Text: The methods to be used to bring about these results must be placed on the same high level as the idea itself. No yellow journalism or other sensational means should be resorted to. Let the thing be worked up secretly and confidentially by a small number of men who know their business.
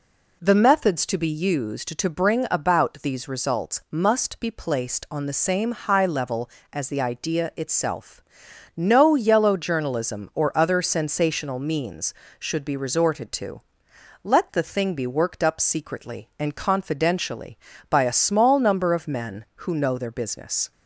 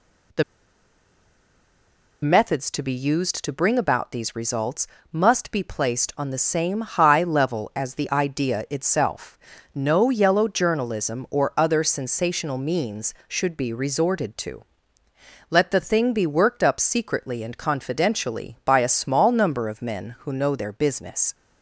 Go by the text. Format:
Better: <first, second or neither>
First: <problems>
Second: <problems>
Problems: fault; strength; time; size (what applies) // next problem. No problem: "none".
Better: first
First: none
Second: pauses between "The" and "methods"; strong; at 0.4 s; 1.8 s long // pauses between "results" and "must"; slight; at 4.8 s; 0.24 s long